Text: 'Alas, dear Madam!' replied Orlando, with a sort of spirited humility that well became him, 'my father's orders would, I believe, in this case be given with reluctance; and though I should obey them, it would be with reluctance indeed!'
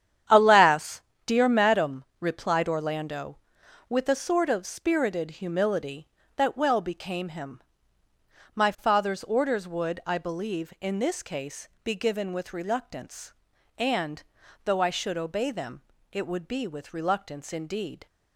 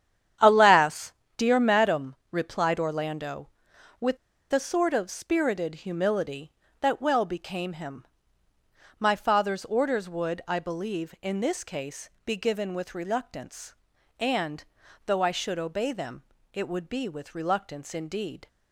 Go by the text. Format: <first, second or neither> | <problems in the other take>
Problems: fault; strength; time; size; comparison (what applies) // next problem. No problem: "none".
first | starts louder than the rest; strong; until 1.6 s; 9.5 dB; strong in the first // pauses between "with" and "a"; at 4.1 s; 0.36 s long // pauses between "case" and "be"; slight; at 12.0 s; 0.16 s long; slight in the first // pauses between "and" and "though"; at 14.6 s; 0.44 s long; also in the first